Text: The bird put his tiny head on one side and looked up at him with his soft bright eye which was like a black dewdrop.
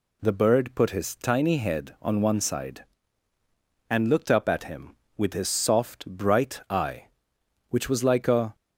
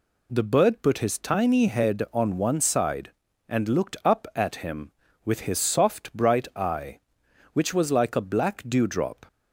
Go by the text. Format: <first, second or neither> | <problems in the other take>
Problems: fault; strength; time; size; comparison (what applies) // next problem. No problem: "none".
second | stops before "black dewdrop"; at 8.5 s